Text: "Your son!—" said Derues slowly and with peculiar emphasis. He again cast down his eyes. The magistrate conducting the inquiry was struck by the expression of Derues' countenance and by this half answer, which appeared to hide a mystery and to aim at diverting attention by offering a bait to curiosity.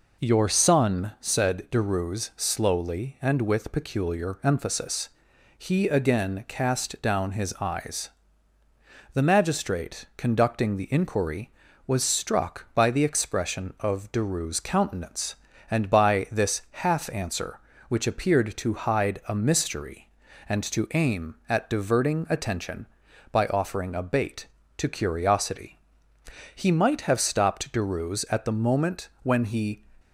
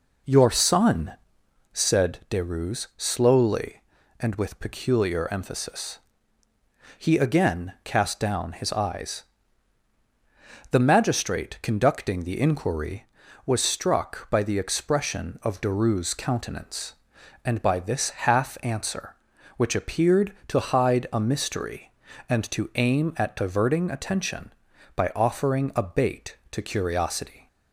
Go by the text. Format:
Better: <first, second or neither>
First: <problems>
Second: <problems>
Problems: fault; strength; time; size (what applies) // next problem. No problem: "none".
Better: second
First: goes on to say "He might have stopped Derues at the moment when he"; strong; from 26.5 s on; 3.2 s long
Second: none